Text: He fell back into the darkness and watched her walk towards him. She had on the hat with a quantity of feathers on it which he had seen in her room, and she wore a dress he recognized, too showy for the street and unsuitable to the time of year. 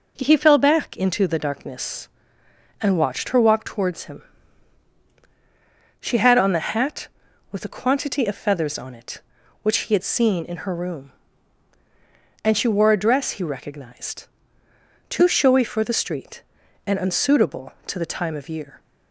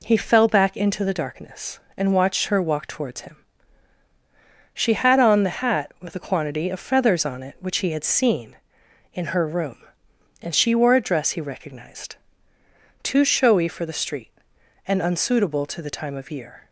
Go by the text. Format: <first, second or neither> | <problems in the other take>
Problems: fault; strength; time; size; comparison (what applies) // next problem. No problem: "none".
neither | none